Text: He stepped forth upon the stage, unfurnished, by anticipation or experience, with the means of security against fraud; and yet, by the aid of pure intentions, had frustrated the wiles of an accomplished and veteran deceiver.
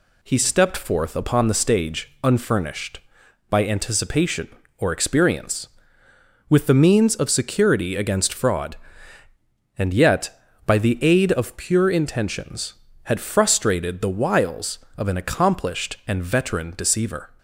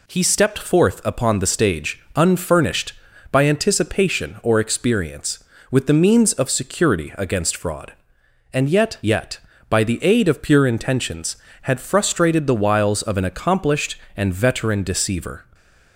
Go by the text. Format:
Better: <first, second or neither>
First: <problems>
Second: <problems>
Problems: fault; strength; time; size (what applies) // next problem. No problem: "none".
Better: first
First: none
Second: says "yet" twice; at 9.0 s // stays silent after the last word; slight; from 15.4 s on; 0.5 s long